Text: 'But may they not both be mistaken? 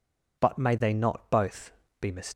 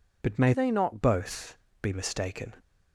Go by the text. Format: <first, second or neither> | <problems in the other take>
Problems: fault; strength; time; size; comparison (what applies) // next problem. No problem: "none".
first | changes voice from "they" to "not"; from 0.5 to 1.0 s; 0.5 s long // pauses between "both" and "be"; slight; at 1.5 s; 0.24 s long; slight in the first